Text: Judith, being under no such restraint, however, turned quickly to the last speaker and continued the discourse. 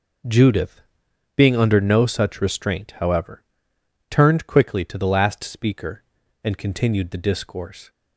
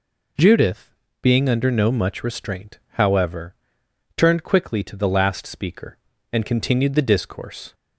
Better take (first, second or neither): first